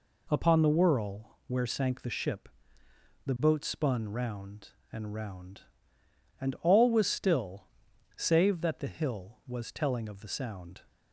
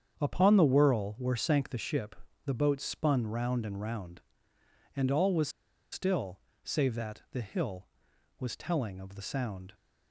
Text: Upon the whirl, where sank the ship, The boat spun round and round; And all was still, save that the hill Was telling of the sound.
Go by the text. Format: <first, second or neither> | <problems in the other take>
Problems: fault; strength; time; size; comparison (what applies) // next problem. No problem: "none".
first | starts louder than the rest; strong; until 1.2 s; 7.5 dB // pauses between "was" and "still"; at 5.4 s; 0.42 s long